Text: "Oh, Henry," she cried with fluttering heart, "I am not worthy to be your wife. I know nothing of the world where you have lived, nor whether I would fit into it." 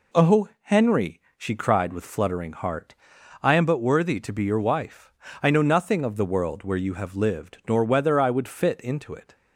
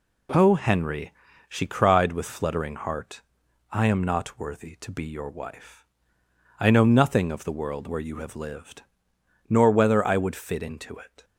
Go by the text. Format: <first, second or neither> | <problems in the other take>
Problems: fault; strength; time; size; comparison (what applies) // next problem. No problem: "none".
second | says "but" for "not"; at 3.6 s